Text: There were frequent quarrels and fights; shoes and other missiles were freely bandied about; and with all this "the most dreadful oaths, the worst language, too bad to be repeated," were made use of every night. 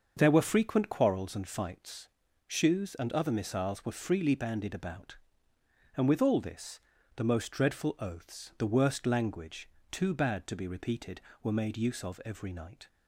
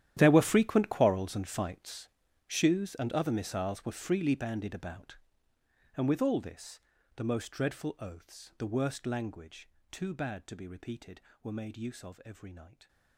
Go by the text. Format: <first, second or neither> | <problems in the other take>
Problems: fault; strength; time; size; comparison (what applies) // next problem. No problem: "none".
first | gets quieter; strong; throughout; 18 dB // starts louder than the rest; strong; until 1.1 s; 11.5 dB; also in the first // pauses between "this" and "the"; at 6.7 s; 0.38 s long; also in the first